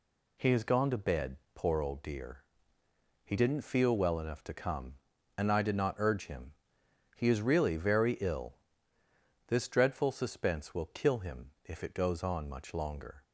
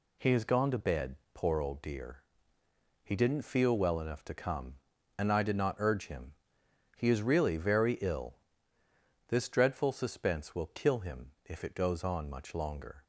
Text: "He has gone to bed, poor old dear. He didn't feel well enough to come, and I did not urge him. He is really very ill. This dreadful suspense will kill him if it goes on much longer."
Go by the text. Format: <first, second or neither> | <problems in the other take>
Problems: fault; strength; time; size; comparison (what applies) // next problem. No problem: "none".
neither | none